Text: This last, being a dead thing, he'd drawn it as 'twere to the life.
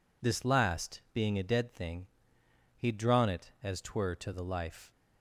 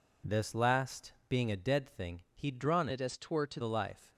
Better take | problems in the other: first | changes voice from "it" to "to"; from 2.9 to 3.6 s; 0.7 s long

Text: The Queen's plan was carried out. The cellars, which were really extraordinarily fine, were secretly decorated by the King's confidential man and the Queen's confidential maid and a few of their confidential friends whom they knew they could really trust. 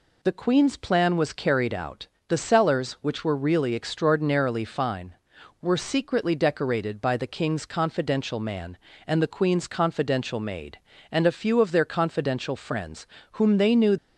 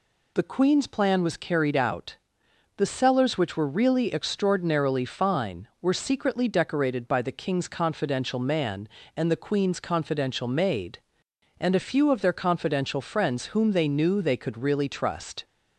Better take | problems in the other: second | pauses between "friends" and "whom"; slight; at 13.0 s; 0.26 s long // stops before "they could really trust"; at 13.9 s

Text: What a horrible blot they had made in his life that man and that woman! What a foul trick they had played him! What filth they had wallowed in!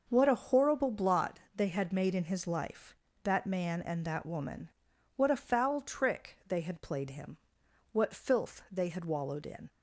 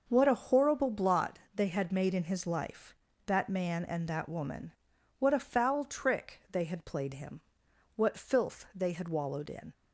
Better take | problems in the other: neither | pauses between "blot" and "they"; slight; the same in both

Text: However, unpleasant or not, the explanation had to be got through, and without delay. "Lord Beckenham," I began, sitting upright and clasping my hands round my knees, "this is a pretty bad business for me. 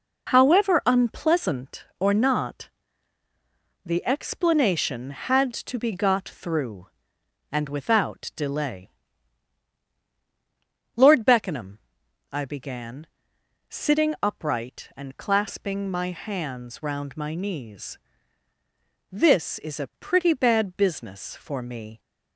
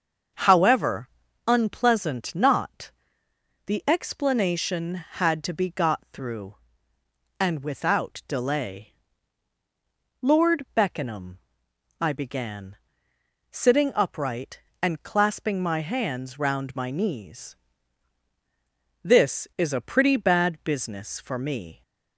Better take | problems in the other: first | starts louder than the rest; until 1.7 s; 6.5 dB // skips "or"; at 2.3 s

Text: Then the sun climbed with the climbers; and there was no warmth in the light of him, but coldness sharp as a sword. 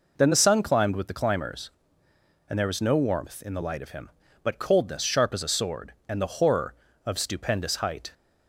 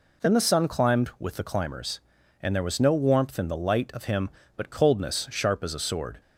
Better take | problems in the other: second | goes on to say "And the horror of stupendous height"; strong; from 6.0 s on; 2.0 s long

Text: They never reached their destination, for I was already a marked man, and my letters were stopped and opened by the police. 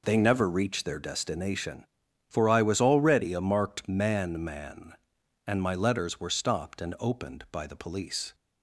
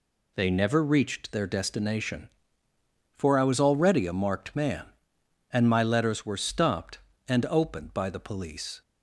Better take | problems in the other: second | says "man" twice; at 4.4 s

